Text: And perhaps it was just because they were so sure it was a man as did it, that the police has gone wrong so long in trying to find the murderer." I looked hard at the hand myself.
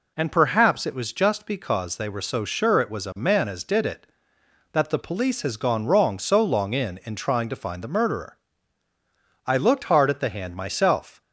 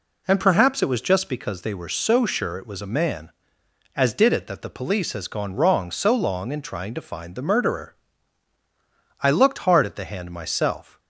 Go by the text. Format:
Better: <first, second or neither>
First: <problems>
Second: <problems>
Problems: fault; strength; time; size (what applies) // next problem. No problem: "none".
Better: second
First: says "in" twice; at 7.0 s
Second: none